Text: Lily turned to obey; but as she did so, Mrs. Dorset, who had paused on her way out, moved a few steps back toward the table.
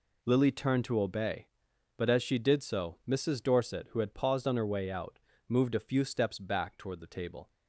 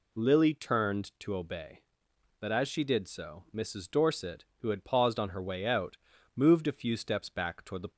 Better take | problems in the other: first | stops before "table"; at 7.9 s

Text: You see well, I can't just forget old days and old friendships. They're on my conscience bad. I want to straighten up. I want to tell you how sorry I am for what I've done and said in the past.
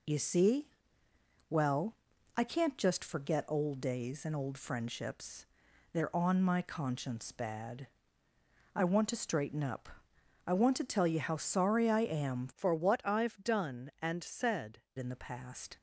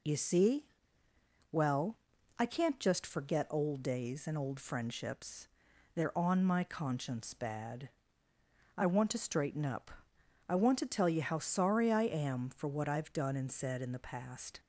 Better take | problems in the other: second | pauses between "see" and "well"; noticeable; at 0.6 s; 0.80 s long; noticeable in the second // changes voice from "for" to "said"; from 12.5 to 14.8 s; 2.3 s long

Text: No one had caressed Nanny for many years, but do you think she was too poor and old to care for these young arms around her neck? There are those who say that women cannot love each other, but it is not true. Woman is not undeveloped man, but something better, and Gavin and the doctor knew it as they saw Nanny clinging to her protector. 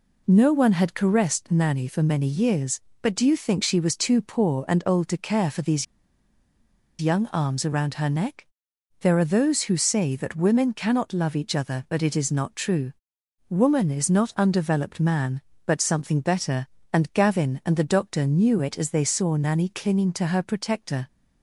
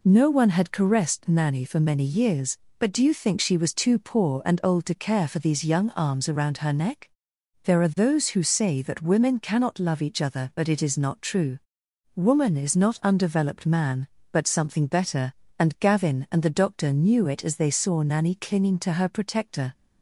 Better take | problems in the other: second | pauses between "these" and "young"; at 5.8 s; 1.1 s long

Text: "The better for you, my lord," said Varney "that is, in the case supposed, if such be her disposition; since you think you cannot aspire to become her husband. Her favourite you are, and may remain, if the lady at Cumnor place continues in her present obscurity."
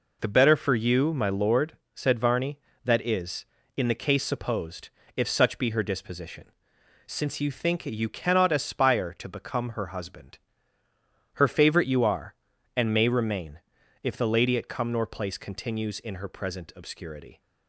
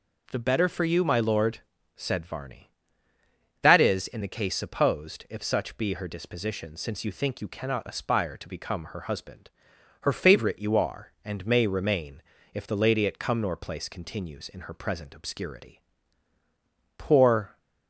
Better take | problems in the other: first | goes on to say "Poor"; noticeable; from 16.9 s on; 0.62 s long

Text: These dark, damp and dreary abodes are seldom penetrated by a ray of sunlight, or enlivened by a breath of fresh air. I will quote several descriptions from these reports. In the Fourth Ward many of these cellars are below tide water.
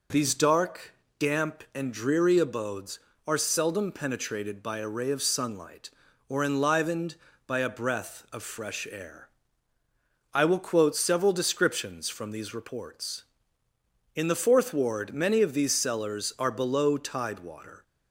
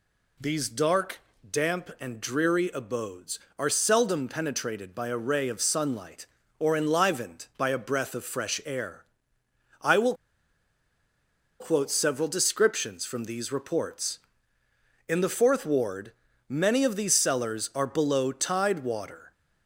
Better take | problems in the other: first | pauses between "will" and "quote"; strong; at 10.1 s; 1.4 s long // pauses between "Ward" and "many"; slight; at 16.1 s; 0.36 s long

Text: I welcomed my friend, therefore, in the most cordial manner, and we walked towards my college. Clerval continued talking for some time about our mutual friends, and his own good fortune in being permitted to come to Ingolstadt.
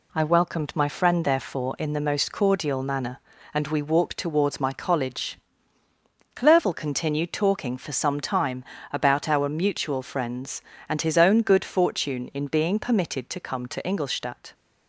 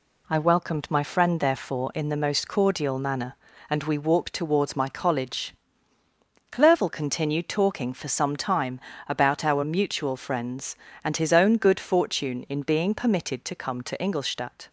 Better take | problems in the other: neither | pauses between "time" and "about"; slight; the same in both

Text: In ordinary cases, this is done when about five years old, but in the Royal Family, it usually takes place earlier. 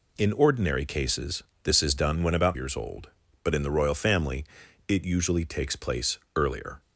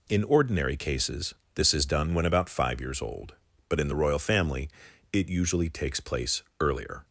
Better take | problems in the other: second | skips "five"; at 2.5 s // pauses between "place" and "earlier"; slight; at 6.1 s; 0.18 s long; slight in the second

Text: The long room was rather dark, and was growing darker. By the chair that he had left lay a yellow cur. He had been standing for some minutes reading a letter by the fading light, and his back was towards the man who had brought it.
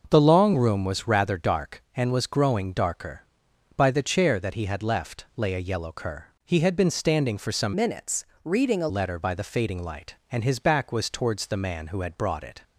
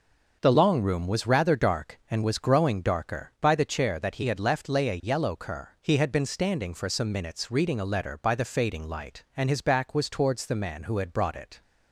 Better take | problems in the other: second | changes voice from "minutes" to "a"; from 7.7 to 8.8 s; 1.1 s long // pauses between "minutes" and "reading"; slight; at 8.2 s; 0.20 s long

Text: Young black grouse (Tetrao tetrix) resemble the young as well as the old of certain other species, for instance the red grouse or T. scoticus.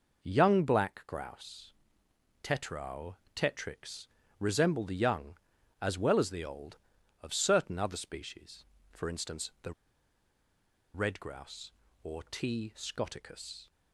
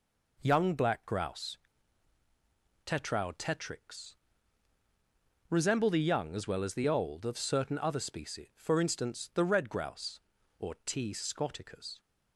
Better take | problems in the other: second | pauses between "Tetrao" and "tetrix"; slight; at 3.1 s; 0.20 s long // pauses between "the" and "red"; at 9.7 s; 1.2 s long

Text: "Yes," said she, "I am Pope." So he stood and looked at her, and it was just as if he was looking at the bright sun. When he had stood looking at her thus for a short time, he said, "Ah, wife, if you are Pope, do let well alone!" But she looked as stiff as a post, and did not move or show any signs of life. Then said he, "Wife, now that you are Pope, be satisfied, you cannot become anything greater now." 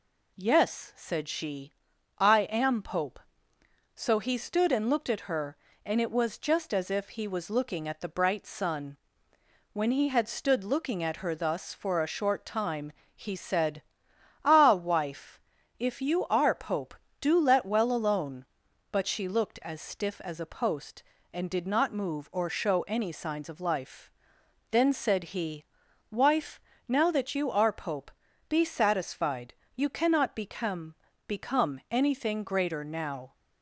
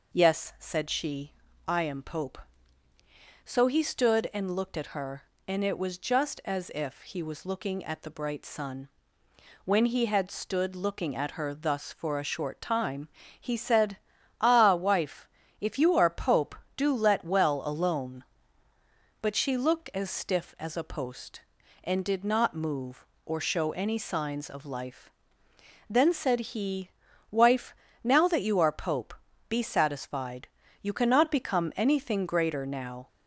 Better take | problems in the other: second | says "become" twice; at 31.2 s

